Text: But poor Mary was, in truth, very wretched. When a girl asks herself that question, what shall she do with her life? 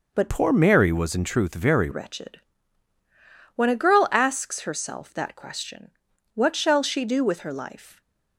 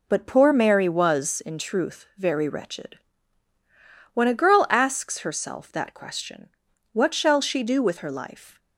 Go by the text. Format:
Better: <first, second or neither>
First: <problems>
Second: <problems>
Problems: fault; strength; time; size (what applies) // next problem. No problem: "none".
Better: second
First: changes voice from "poor" to "very"; from 0.2 to 1.8 s; 1.6 s long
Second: none